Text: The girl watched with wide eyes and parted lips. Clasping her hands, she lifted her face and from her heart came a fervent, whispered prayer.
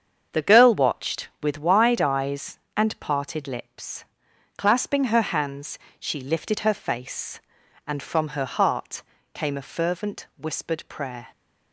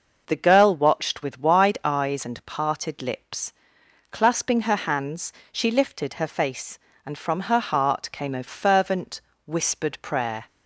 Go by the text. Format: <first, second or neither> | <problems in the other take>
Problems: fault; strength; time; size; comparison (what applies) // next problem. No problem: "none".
second | gets quieter; throughout; 7 dB // pauses between "heart" and "came"; slight; at 9.0 s; 0.30 s long